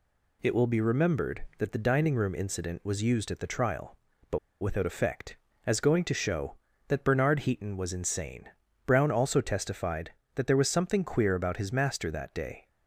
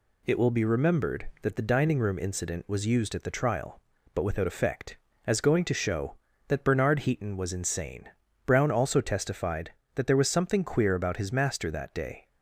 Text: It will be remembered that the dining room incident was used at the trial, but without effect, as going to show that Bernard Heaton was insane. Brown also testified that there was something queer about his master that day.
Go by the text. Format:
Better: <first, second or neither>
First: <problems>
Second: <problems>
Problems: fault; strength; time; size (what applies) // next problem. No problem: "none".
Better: second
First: pauses between "but" and "without"; slight; at 4.3 s; 0.22 s long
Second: none